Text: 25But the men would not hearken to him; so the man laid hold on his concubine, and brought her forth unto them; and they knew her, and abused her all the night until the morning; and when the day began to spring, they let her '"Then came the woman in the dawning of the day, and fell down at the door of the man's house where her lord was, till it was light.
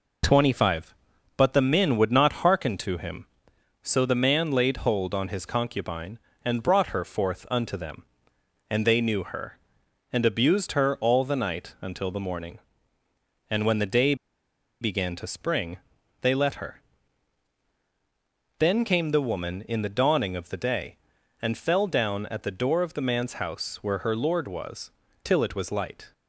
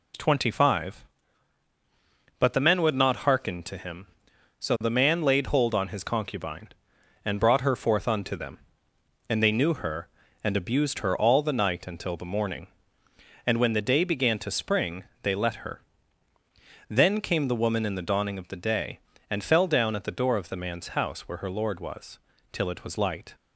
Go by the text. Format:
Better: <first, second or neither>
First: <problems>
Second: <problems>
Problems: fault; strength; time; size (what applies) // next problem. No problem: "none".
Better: second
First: pauses between "day" and "began"; noticeable; at 14.1 s; 0.66 s long // pauses between "her" and "Then"; strong; at 16.8 s; 1.7 s long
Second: pauses between "her" and "Then"; at 15.8 s; 1.0 s long